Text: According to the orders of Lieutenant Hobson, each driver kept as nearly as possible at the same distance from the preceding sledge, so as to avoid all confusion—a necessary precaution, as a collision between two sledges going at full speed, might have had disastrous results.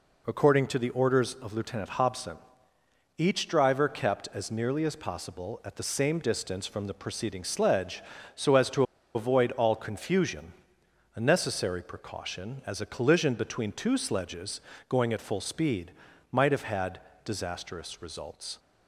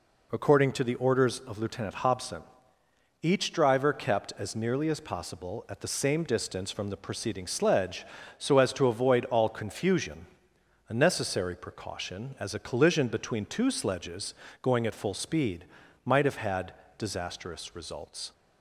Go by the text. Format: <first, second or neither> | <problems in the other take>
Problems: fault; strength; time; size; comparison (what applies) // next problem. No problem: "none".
second | pauses between "to" and "avoid"; slight; at 8.8 s; 0.31 s long // pauses between "sledges" and "going"; slight; at 14.6 s; 0.28 s long; slight in the second // pauses between "had" and "disastrous"; slight; at 17.0 s; 0.24 s long; slight in the second